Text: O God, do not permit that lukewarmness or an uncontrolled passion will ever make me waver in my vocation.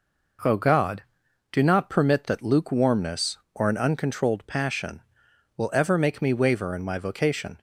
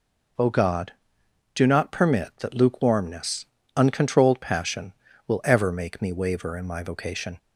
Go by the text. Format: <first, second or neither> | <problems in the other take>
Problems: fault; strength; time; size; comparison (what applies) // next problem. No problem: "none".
first | skips "or an"; at 3.6 s